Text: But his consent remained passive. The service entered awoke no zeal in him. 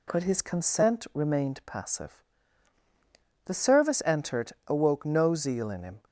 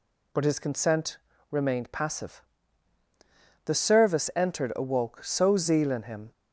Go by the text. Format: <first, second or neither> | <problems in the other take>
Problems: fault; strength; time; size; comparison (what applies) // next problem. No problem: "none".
first | pauses between "consent" and "remained"; slight; at 1.1 s; 0.34 s long // says "so" for "no"; at 5.2 s